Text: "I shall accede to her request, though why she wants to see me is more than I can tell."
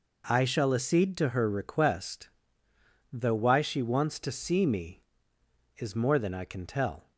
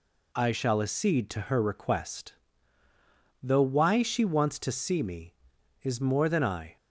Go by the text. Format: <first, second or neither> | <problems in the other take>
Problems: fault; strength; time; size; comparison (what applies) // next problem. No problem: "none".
first | stops before "can tell"; at 6.7 s